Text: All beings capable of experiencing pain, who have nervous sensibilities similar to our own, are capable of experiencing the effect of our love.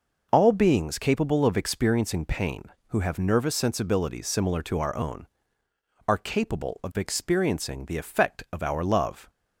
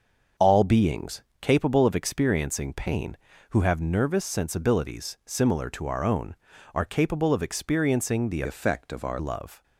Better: first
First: none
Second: starts louder than the rest; until 1.5 s; 6.5 dB // pauses between "beings" and "capable"; slight; at 1.2 s; 0.18 s long // changes voice from "effect" to "our"; from 8.4 to 9.1 s; 0.7 s long

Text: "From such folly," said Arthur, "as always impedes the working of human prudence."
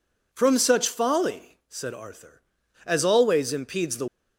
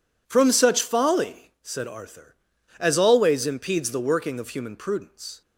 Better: second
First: stops before "working of human prudence"; at 4.0 s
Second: none

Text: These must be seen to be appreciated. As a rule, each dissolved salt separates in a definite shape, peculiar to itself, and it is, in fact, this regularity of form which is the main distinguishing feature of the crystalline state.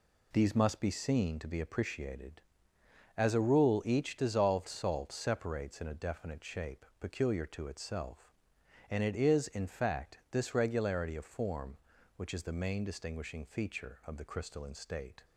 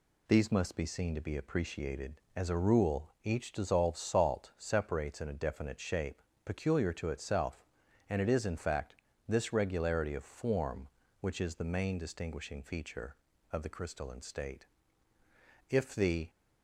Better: first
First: none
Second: goes on to say "If the"; from 15.6 s on; 0.60 s long

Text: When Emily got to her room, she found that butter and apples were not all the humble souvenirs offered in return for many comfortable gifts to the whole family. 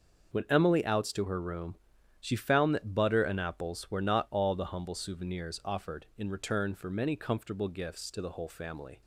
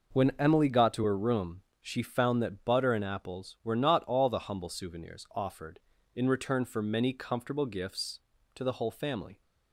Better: second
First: starts louder than the rest; until 1.4 s; 6.5 dB // says "outs" for "got"; at 0.8 s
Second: none

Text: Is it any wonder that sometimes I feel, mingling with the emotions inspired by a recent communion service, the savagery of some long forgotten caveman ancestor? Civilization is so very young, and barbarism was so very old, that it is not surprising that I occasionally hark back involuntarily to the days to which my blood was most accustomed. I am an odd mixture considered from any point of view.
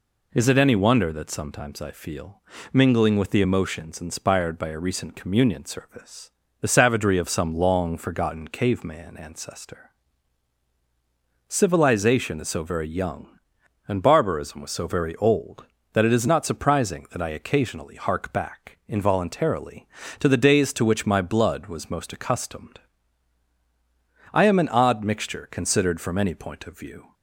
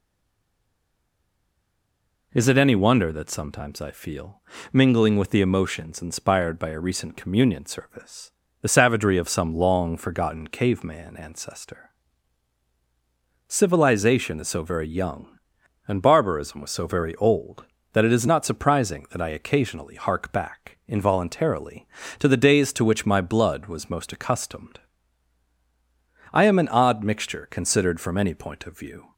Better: first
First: none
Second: stays silent before the first word; until 2.3 s; 2.3 s long

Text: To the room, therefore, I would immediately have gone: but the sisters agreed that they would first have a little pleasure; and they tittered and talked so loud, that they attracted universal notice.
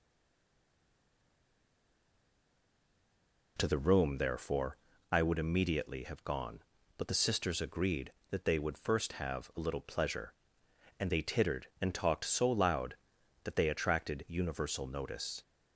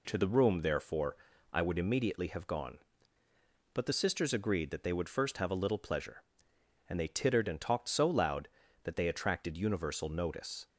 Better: second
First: stays silent before the first word; strong; until 3.5 s; 3.5 s long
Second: none

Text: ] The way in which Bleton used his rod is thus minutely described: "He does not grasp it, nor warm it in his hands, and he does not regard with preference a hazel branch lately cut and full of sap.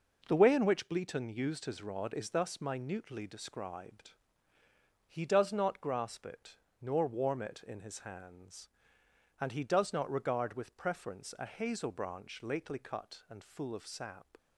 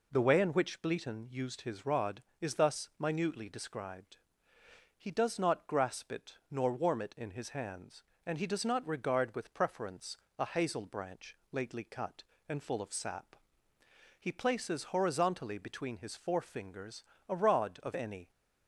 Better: first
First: none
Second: pauses between "preference" and "a"; slight; at 10.1 s; 0.22 s long // pauses between "branch" and "lately"; slight; at 11.3 s; 0.16 s long // goes on to say "He places horizontally between his forefingers a rod of any"; strong; from 14.1 s on; 4.1 s long

